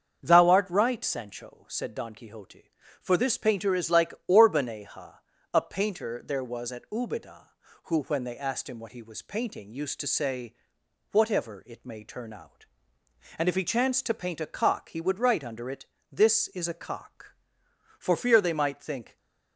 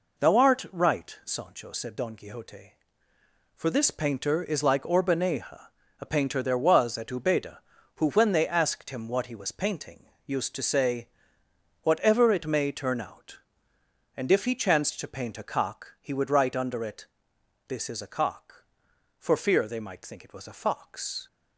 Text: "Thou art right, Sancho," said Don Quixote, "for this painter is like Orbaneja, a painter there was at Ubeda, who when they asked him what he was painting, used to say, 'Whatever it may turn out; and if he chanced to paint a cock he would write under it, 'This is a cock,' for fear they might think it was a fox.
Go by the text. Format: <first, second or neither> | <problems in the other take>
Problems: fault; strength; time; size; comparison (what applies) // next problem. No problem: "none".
second | starts louder than the rest; until 1.2 s; 7 dB // stops before "it was a fox"; at 19.1 s